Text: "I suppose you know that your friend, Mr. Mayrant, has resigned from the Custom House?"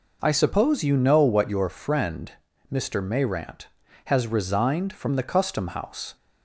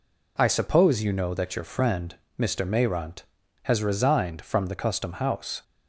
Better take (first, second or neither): second